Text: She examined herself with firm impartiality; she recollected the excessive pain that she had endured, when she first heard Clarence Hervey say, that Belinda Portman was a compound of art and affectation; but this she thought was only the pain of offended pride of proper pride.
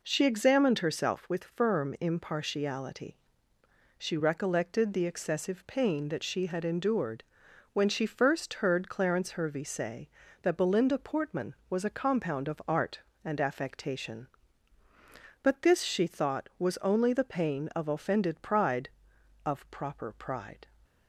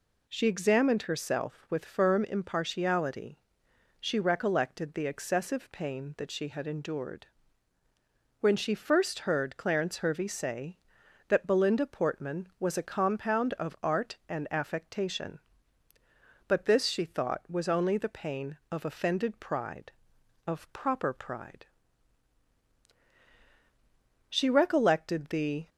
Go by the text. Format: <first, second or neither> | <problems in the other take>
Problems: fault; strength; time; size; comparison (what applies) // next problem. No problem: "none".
first | goes on to say "She recollected the"; from 24.2 s on; 1.4 s long